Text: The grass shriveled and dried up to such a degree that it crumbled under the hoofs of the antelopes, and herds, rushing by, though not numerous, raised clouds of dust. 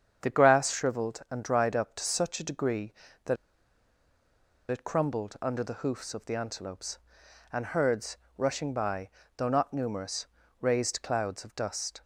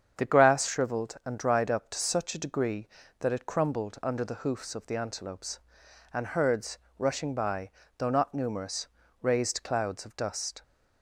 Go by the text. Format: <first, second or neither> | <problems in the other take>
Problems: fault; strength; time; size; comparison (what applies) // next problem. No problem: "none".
second | starts louder than the rest; strong; until 1.3 s; 8 dB; strong in the second // pauses between "that" and "it"; strong; at 3.3 s; 1.3 s long